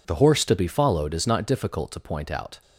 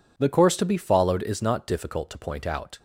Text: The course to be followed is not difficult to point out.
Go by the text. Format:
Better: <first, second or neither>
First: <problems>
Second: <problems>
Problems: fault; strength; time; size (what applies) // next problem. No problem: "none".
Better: second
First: says "horse" for "course"; at 0.1 s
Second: none